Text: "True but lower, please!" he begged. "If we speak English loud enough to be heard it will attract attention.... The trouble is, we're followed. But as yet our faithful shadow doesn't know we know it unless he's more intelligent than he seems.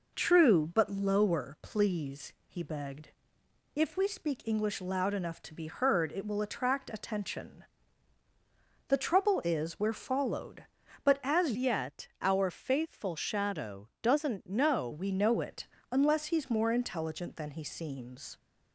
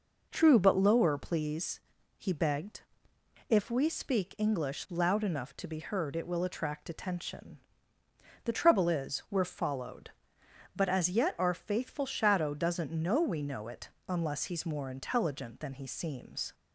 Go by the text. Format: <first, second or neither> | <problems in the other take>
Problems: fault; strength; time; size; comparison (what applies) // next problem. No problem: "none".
second | changes voice from "yet" to "know"; from 11.5 to 14.8 s; 3.3 s long // pauses between "it" and "unless"; slight; at 15.6 s; 0.24 s long; slight in the second